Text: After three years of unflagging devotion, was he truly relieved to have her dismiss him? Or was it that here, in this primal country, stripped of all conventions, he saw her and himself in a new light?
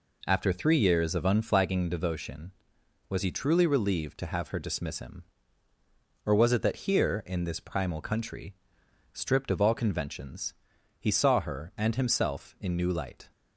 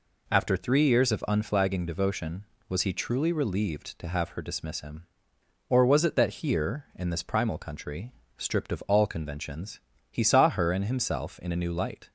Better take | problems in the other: second | skips "a"; at 12.7 s

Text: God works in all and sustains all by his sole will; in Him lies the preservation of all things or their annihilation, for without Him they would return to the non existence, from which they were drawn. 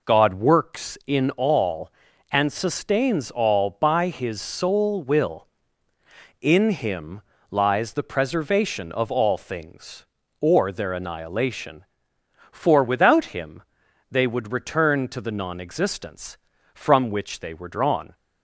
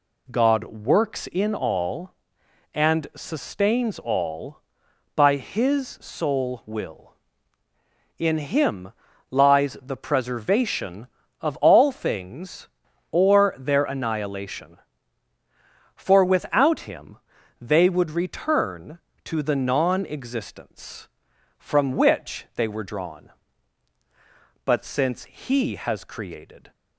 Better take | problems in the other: first | pauses between "Him" and "lies"; at 8.9 s; 0.40 s long; slight in the first // pauses between "Him" and "they"; at 17.1 s; 0.44 s long; noticeable in the first // goes on to say "But since He has created"; strong; from 24.6 s on; 2.0 s long

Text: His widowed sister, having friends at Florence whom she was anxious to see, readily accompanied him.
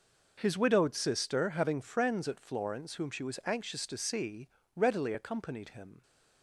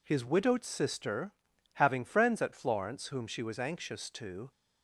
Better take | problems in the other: first | stops before "see readily accompanied him"; at 4.5 s

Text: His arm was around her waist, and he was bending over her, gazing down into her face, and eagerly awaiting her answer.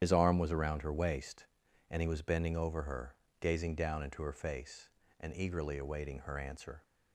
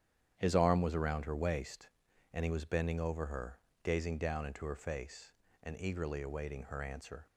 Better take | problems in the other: second | loses the start of "His"; at 0.0 s; 65 ms // starts louder than the rest; strong; until 1.0 s; 9.5 dB; strong in the second

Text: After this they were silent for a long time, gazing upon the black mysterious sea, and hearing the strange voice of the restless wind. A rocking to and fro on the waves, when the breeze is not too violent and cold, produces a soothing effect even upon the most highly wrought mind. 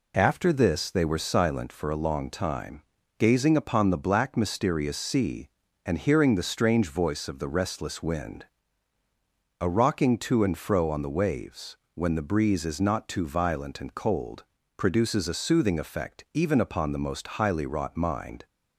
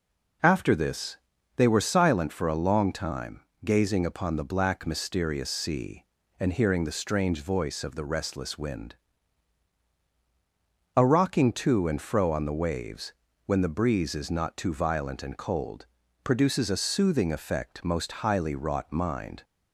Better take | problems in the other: first | pauses between "this" and "they"; at 1.1 s; 0.38 s long // skips "even upon the"; at 17.8 s

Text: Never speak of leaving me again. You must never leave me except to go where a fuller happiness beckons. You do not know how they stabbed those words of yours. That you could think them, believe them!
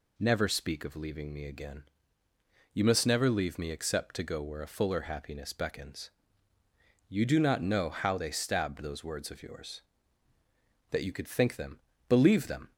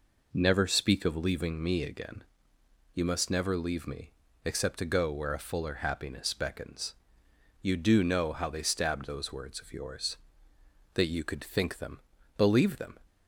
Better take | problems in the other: first | pauses between "me" and "except"; slight; at 4.1 s; 0.32 s long // skips "not"; at 8.0 s

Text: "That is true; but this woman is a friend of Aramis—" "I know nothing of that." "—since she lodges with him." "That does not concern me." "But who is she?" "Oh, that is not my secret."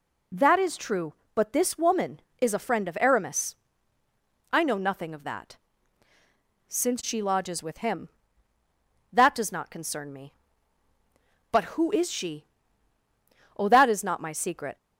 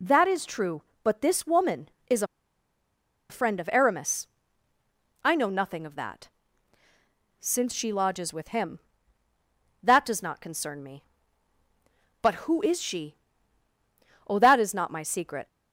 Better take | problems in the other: first | pauses between "is" and "a"; at 2.2 s; 1.0 s long

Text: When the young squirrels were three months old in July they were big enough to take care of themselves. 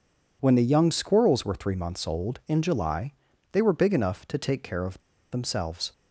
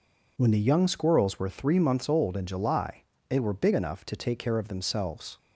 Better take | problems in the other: second | pauses between "July" and "they"; at 3.1 s; 0.40 s long; slight in the second // pauses between "of" and "themselves"; slight; at 4.9 s; 0.33 s long

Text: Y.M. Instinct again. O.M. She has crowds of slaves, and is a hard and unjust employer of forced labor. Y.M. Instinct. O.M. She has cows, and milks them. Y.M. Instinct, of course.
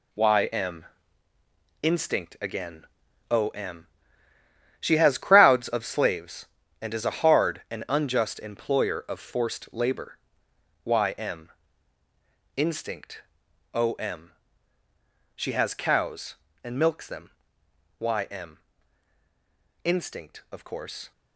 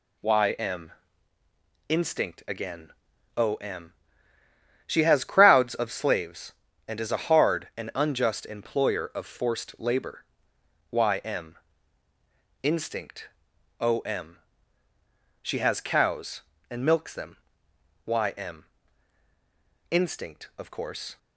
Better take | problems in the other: second | gets quieter; strong; throughout; 8 dB

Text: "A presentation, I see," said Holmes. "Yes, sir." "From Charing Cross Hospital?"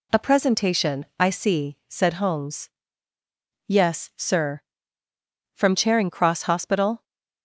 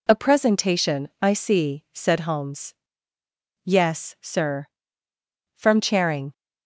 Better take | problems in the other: first | stops before "Cross Hospital"; at 6.3 s

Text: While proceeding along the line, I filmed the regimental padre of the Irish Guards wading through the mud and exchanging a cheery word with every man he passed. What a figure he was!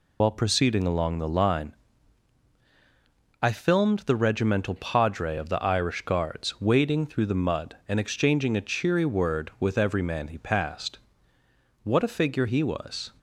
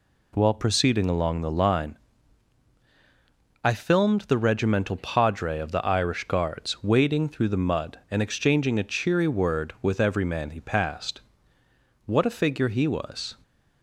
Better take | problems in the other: second | loses the start of "While"; at 0.2 s; 100 ms

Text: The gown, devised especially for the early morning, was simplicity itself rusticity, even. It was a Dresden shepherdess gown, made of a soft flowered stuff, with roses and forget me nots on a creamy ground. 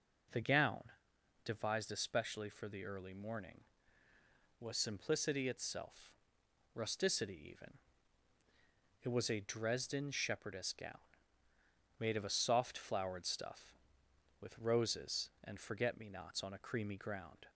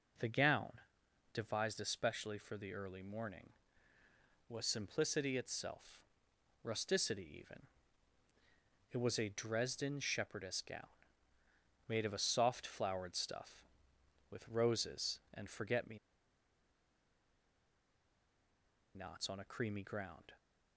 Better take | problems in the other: first | pauses between "itself" and "rusticity"; noticeable; at 6.0 s; 0.60 s long; noticeable in the first // pauses between "me" and "nots"; strong; at 15.9 s; 2.9 s long

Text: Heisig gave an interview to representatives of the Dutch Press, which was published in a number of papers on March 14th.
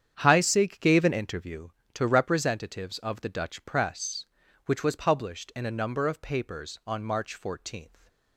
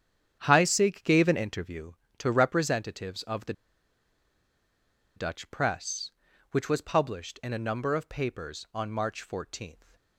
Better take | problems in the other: first | starts louder than the rest; strong; until 1.4 s; 9 dB; strong in the first // pauses between "the" and "Dutch"; strong; at 3.5 s; 1.6 s long

